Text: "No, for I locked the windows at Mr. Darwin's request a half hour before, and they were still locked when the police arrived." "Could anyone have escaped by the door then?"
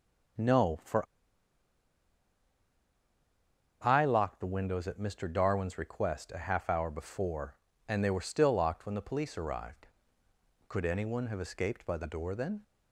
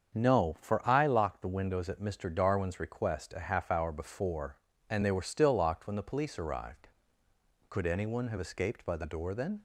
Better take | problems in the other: second | starts louder than the rest; strong; until 4.2 s; 7.5 dB; strong in the second // pauses between "for" and "I"; strong; at 1.0 s; 2.8 s long

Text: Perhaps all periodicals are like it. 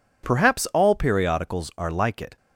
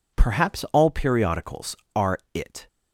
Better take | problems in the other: first | skips "like"; at 2.2 s

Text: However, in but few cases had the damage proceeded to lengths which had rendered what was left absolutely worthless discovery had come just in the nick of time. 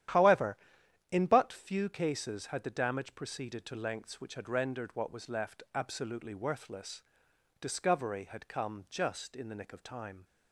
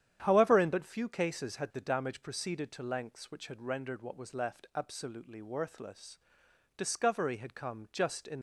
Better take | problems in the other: first | starts louder than the rest; strong; until 1.2 s; 9.5 dB; strong in the first // pauses between "worthless" and "discovery"; noticeable; at 6.1 s; 0.58 s long; noticeable in the first // stops before "the nick of time"; at 8.3 s

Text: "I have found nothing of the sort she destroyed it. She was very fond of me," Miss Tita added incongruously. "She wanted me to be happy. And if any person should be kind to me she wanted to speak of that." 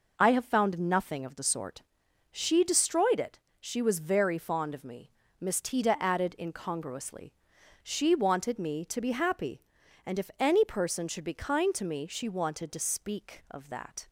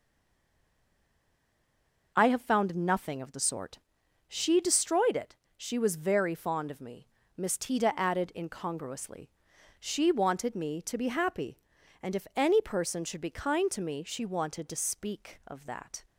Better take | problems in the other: first | stays silent before the first word; until 2.1 s; 2.1 s long // pauses between "sort" and "she"; noticeable; at 3.7 s; 0.50 s long; noticeable in the first

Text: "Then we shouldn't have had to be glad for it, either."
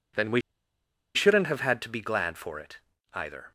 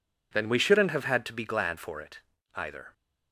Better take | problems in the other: second | pauses between "we" and "shouldn't"; noticeable; at 0.4 s; 0.74 s long

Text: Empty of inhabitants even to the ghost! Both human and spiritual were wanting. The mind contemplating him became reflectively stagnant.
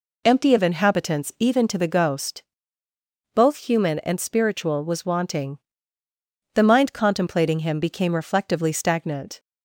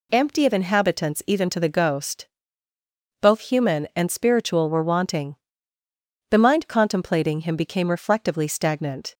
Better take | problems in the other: second | says "was" for "were"; at 4.8 s

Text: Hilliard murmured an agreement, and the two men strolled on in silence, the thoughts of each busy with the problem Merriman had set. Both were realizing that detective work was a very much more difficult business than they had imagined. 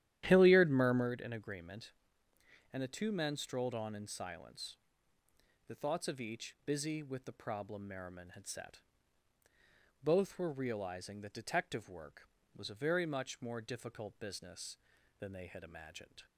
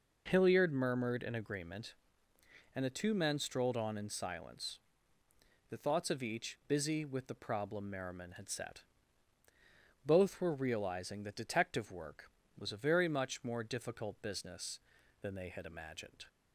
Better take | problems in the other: second | starts louder than the rest; strong; until 1.1 s; 12 dB

